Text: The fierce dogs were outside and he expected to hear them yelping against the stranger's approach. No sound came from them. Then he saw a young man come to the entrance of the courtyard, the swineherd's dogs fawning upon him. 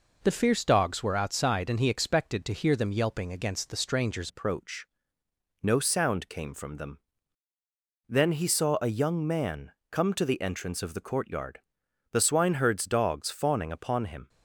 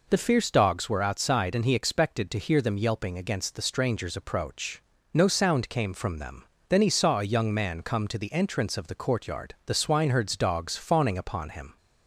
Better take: second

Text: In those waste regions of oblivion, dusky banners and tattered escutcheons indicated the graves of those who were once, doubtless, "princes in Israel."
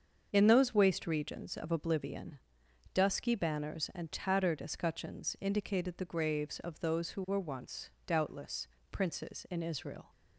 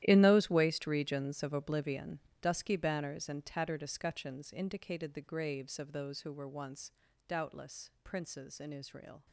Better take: first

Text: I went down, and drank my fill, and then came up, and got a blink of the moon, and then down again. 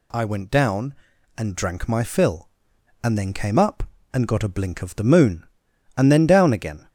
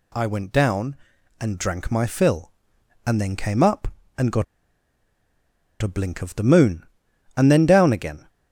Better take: first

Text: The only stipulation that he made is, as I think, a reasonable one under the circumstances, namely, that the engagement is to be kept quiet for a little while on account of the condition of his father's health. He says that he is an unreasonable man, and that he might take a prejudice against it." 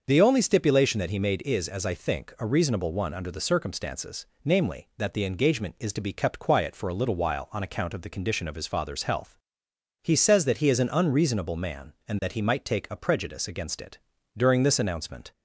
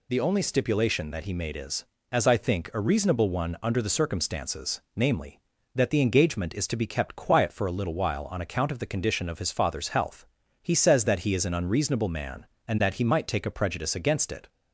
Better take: second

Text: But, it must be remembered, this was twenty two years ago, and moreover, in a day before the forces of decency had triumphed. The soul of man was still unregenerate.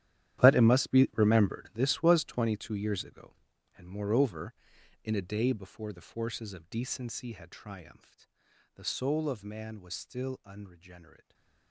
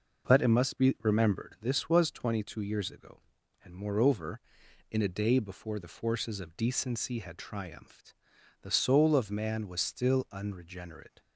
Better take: second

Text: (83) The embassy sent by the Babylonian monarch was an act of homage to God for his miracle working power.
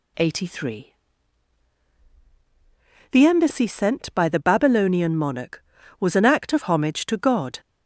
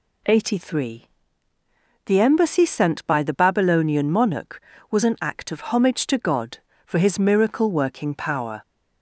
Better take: second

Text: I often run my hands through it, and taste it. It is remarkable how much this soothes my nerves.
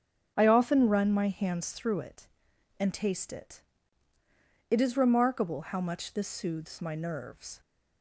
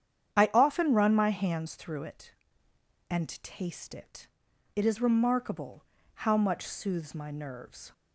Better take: first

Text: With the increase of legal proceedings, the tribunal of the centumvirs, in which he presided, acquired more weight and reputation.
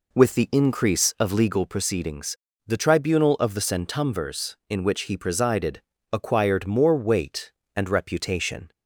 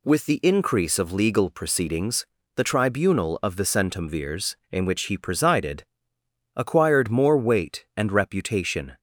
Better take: second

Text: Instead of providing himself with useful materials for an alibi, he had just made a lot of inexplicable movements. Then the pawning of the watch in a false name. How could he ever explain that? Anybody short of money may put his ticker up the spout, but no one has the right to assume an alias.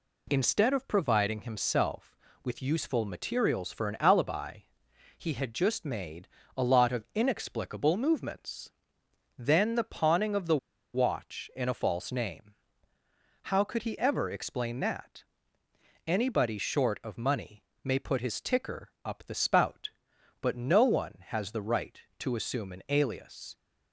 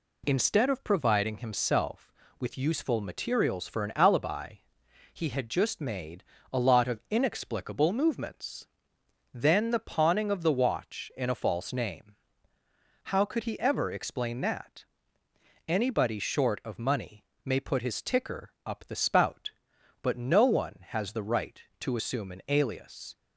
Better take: second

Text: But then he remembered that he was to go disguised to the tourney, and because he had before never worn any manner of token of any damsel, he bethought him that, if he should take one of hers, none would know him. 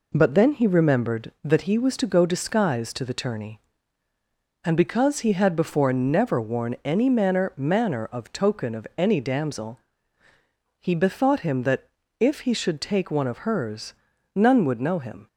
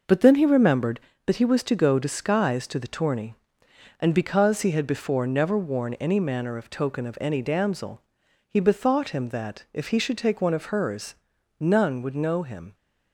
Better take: second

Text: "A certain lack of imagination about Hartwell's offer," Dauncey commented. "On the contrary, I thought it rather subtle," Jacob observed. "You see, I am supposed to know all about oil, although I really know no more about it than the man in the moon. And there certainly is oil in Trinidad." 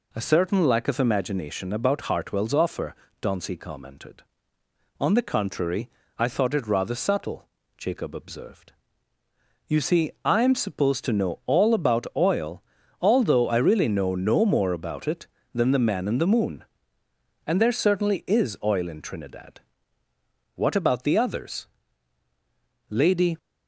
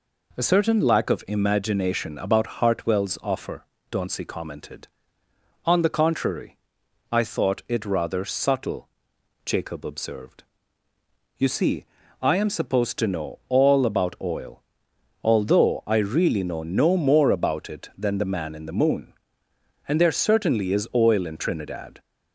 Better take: second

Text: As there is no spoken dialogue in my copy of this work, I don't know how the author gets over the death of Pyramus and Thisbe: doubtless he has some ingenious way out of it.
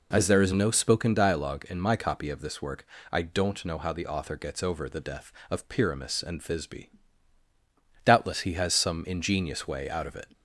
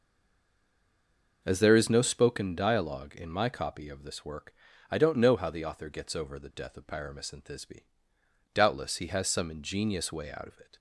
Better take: first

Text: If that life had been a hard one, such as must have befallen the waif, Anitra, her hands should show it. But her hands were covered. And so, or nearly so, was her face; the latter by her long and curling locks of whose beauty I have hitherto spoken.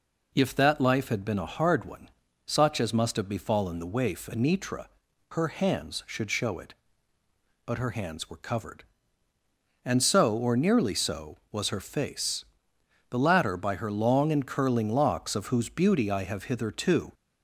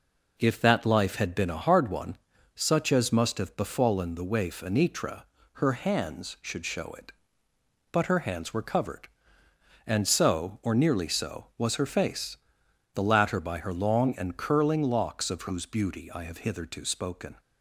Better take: second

